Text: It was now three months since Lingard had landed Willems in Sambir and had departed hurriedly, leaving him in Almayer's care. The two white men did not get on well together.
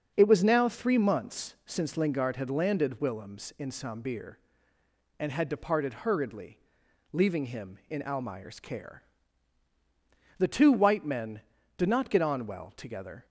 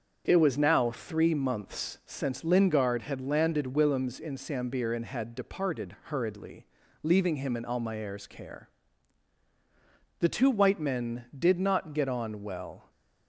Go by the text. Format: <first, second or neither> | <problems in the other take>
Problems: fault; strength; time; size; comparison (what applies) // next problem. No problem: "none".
first | starts louder than the rest; until 1.2 s; 6.5 dB; also in the first // stops before "together"; at 12.9 s